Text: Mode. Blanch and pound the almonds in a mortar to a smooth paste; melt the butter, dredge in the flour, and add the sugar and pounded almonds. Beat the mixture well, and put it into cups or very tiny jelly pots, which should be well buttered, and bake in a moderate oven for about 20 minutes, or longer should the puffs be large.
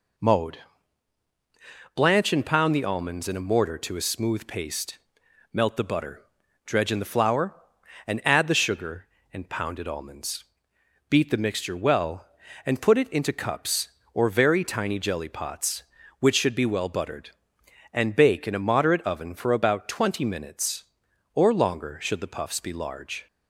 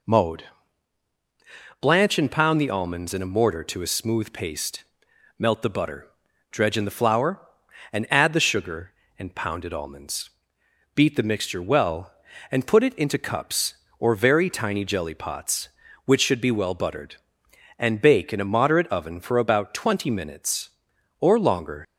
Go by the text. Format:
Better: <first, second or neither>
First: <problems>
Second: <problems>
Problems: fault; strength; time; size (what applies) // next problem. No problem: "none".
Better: first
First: none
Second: stops before "should the puffs be large"; at 21.8 s